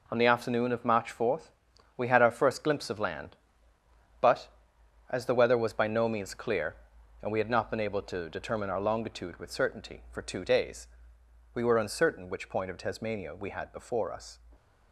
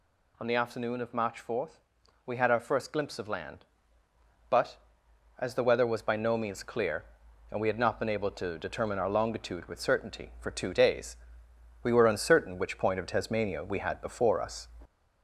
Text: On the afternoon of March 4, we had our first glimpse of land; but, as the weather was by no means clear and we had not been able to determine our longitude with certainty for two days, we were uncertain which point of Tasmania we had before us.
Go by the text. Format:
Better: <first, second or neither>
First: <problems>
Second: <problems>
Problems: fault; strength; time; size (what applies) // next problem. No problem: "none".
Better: first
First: none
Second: gets louder; slight; throughout; 2.5 dB